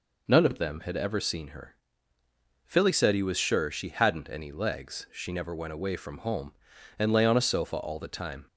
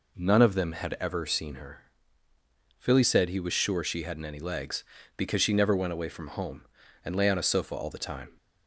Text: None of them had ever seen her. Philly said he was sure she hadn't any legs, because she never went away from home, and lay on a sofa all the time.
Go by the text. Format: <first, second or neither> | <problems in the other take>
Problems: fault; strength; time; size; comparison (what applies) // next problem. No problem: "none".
second | skips "because"; at 5.0 s